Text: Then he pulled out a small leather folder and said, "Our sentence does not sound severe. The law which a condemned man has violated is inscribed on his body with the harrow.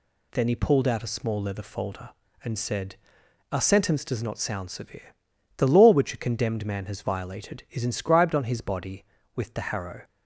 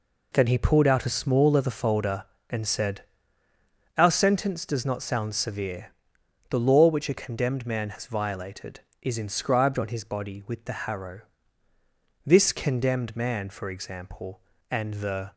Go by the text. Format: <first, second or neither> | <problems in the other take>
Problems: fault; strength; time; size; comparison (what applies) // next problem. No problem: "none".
first | goes on to say "This Condemned Man for example and the"; strong; from 12.2 s on; 3.0 s long